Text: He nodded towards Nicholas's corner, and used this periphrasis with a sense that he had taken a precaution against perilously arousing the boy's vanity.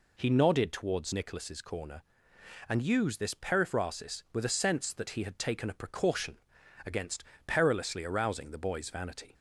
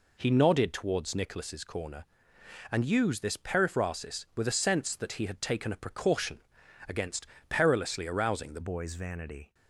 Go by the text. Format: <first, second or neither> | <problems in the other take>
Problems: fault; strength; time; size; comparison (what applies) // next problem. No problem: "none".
first | pauses between "precaution" and "against"; noticeable; at 6.4 s; 0.48 s long; noticeable in the first // pauses between "against" and "perilously"; slight; at 7.2 s; 0.24 s long; slight in the first // changes voice at "boy's"; from 8.6 s on; 0.9 s long